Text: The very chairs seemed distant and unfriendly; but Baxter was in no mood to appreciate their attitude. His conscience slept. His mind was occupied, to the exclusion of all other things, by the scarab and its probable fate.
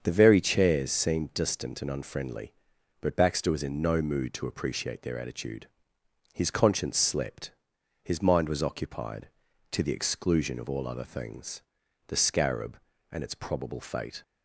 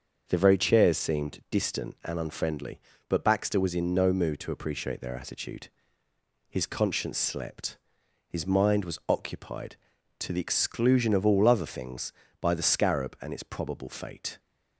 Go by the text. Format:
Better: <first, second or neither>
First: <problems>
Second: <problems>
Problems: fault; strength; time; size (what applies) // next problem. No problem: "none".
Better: second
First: starts louder than the rest; until 1.0 s; 7 dB // skips "by"; at 11.8 s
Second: starts louder than the rest; until 1.2 s; 6.5 dB